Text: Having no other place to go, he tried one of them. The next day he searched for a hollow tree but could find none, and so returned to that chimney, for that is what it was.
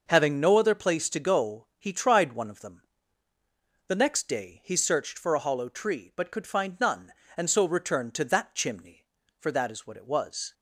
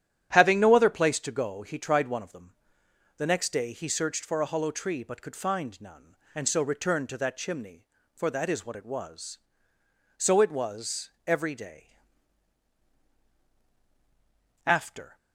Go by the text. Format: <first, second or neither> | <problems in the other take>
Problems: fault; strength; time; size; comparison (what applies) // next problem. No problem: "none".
first | starts louder than the rest; strong; until 1.3 s; 11 dB // goes on to say "So it was every day After"; strong; from 10.1 s on; 4.9 s long